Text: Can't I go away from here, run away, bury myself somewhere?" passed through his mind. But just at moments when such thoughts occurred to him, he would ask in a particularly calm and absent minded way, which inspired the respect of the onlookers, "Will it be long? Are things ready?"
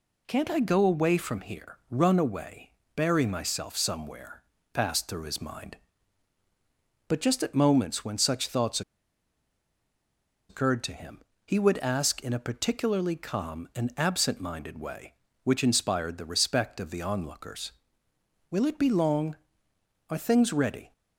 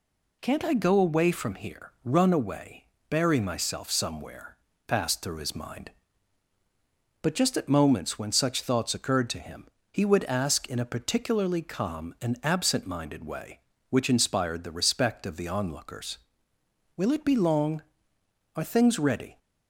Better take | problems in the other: second | pauses between "thoughts" and "occurred"; strong; at 8.8 s; 1.6 s long

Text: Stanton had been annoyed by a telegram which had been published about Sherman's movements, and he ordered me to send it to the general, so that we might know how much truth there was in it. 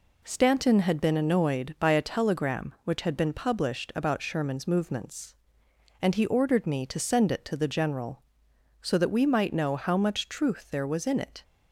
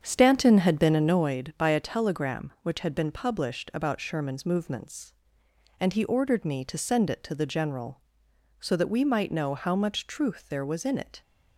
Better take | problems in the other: first | starts louder than the rest; strong; until 1.3 s; 7.5 dB

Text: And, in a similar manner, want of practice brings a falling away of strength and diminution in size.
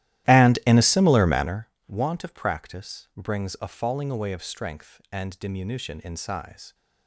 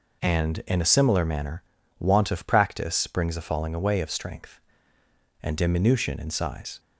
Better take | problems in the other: second | starts louder than the rest; strong; until 1.7 s; 14 dB

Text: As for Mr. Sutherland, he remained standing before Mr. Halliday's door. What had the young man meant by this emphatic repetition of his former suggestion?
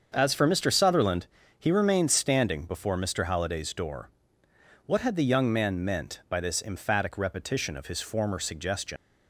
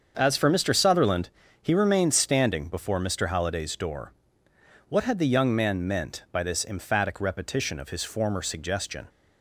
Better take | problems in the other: second | starts louder than the rest; until 1.1 s; 7 dB; also in the second // leaves "suggestion" unfinished; at 8.9 s; 100 ms

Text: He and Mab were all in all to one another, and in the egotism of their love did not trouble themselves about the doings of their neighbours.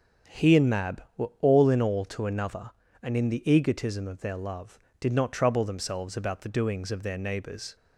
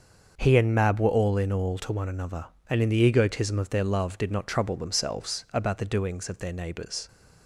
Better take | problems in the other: second | starts louder than the rest; until 1.5 s; 6 dB; also in the second // skips "one"; at 2.2 s

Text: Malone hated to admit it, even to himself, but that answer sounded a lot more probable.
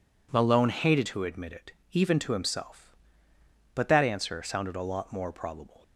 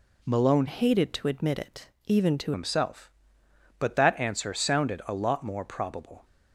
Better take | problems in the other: first | changes voice from "hated" to "to"; from 0.6 to 2.5 s; 1.9 s long

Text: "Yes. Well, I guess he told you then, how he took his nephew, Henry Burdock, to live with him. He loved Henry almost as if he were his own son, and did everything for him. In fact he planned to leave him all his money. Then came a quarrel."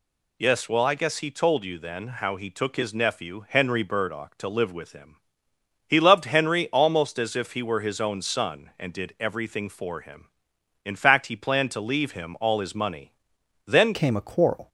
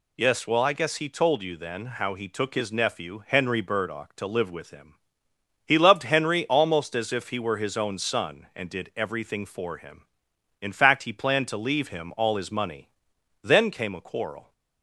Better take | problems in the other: second | changes voice at "came"; from 13.9 s on; 0.7 s long

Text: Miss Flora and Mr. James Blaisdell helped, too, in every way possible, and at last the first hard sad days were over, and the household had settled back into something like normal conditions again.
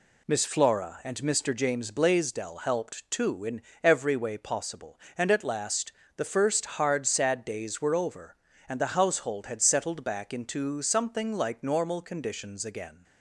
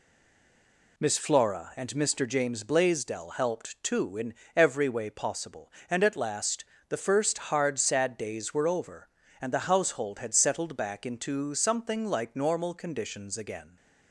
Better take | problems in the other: first | stays silent before the first word; until 0.9 s; 0.9 s long // pauses between "in" and "every"; slight; at 4.3 s; 0.24 s long; slight in the first // pauses between "last" and "the"; slight; at 6.6 s; 0.24 s long; slight in the first

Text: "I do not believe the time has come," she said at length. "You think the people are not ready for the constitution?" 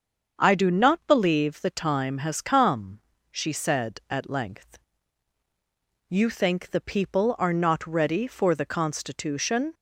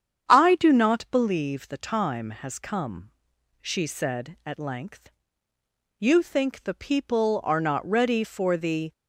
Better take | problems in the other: first | starts louder than the rest; strong; until 1.3 s; 8.5 dB; also in the first // stops before "constitution"; at 8.9 s

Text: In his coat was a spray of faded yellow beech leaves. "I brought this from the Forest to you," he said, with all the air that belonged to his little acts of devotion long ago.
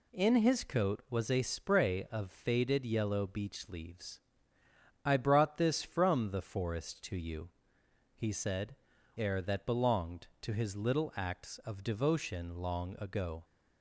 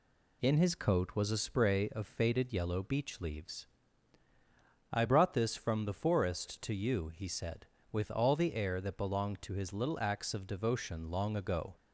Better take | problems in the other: second | skips "with all the"; at 8.9 s

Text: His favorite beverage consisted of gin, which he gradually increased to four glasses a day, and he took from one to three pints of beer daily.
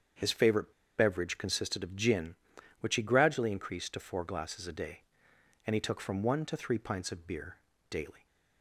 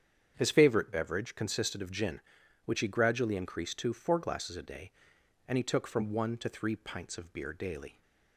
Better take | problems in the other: second | starts louder than the rest; strong; until 1.4 s; 7.5 dB; strong in the second // pauses between "favorite" and "beverage"; slight; at 0.7 s; 0.26 s long // pauses between "beer" and "daily"; slight; at 7.5 s; 0.32 s long

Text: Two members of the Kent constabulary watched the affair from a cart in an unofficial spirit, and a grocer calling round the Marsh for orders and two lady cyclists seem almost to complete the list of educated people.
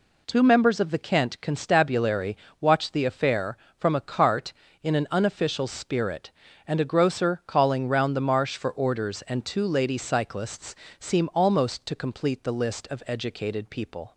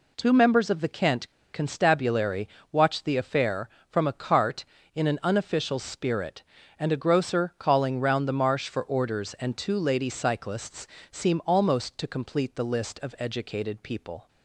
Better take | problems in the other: first | pauses between "Kent" and "constabulary"; slight; at 1.2 s; 0.25 s long // pauses between "constabulary" and "watched"; slight; at 2.4 s; 0.24 s long; slight in the first // pauses between "cyclists" and "seem"; slight; at 10.8 s; 0.24 s long; slight in the first

